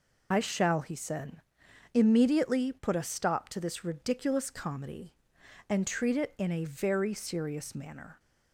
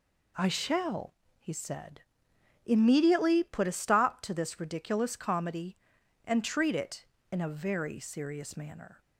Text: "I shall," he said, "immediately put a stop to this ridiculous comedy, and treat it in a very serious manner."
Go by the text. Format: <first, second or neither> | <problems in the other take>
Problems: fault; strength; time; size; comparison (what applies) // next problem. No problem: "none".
second | loses the start of "I"; at 0.3 s; 60 ms